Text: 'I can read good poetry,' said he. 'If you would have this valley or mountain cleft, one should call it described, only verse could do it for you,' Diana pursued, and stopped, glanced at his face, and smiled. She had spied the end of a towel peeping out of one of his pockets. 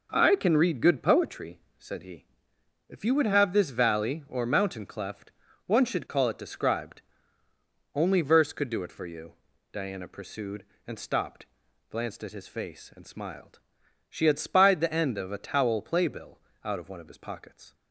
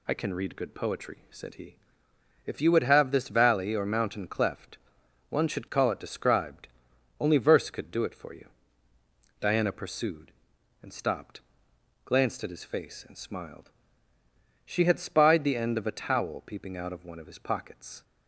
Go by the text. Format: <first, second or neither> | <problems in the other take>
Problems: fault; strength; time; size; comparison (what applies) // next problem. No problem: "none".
second | says "playbill" for "peeping"; at 15.7 s